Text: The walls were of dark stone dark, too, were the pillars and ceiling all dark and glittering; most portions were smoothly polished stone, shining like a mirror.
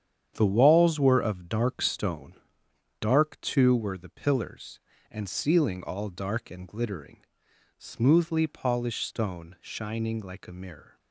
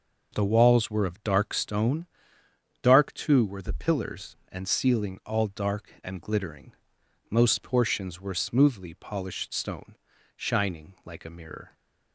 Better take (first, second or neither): second